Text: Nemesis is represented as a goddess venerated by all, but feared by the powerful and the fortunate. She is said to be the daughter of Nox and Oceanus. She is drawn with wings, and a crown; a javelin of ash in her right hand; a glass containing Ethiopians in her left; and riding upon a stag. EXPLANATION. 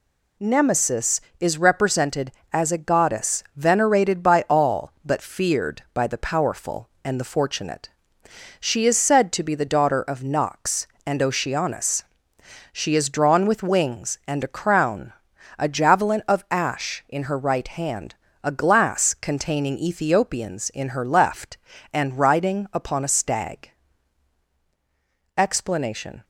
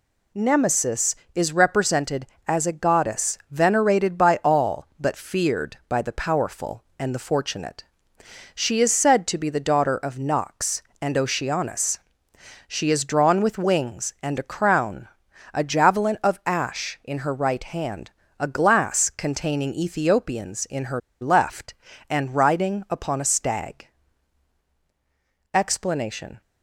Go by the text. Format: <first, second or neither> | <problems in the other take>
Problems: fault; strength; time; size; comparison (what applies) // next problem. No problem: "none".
first | pauses between "her" and "left"; slight; at 20.9 s; 0.21 s long